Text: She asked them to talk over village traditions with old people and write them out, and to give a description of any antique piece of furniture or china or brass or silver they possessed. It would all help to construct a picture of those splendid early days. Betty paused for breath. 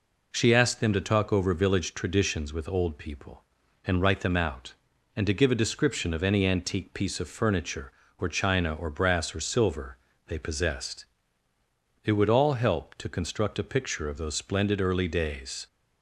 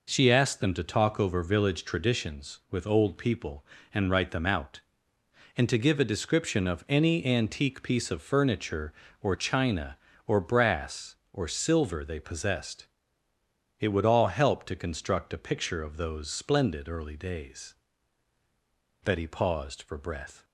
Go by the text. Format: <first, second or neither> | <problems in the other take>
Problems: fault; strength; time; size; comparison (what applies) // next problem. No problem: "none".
second | pauses between "silver" and "they"; slight; at 9.9 s; 0.30 s long // stops before "Betty paused for breath"; at 15.6 s